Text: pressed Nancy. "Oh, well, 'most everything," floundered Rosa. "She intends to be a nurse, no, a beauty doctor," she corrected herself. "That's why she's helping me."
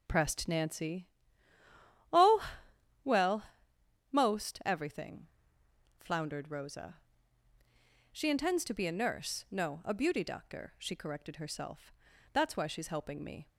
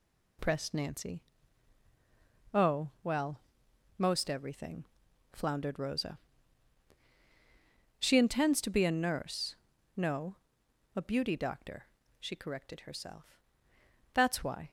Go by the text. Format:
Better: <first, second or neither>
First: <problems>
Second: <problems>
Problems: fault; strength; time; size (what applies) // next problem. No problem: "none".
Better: first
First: none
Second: stops before "she's helping me"; at 14.6 s